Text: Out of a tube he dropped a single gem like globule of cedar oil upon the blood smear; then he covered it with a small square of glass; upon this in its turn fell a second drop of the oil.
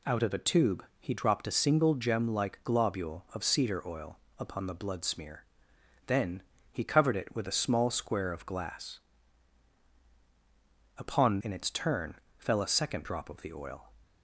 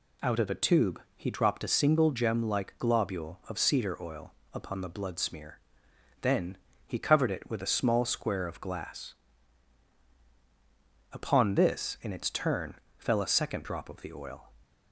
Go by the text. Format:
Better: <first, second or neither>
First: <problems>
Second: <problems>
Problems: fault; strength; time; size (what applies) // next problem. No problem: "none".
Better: second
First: pauses between "tube" and "he"; slight; at 0.8 s; 0.16 s long // pauses between "oil" and "upon"; slight; at 4.1 s; 0.20 s long // pauses between "then" and "he"; slight; at 6.4 s; 0.30 s long // skips "this"; at 11.4 s // pauses between "turn" and "fell"; slight; at 12.1 s; 0.18 s long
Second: pauses between "tube" and "he"; slight; at 0.9 s; 0.16 s long // pauses between "oil" and "upon"; slight; at 4.3 s; 0.20 s long // pauses between "then" and "he"; slight; at 6.5 s; 0.30 s long // pauses between "turn" and "fell"; slight; at 12.7 s; 0.18 s long